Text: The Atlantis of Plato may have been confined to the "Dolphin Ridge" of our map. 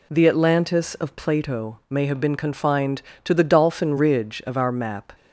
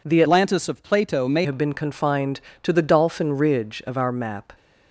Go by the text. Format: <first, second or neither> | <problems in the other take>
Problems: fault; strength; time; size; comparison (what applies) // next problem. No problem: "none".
first | changes voice from "Atlantis" to "may"; from 0.2 to 1.4 s; 1.2 s long